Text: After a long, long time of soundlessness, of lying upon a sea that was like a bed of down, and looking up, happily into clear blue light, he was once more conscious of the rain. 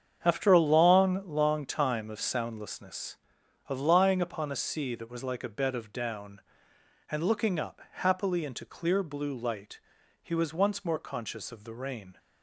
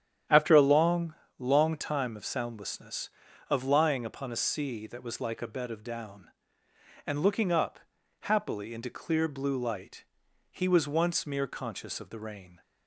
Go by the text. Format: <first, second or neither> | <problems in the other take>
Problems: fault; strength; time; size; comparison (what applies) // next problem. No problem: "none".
first | starts louder than the rest; strong; until 1.5 s; 9.5 dB; strong in the first // says "mere" for "more"; at 11.2 s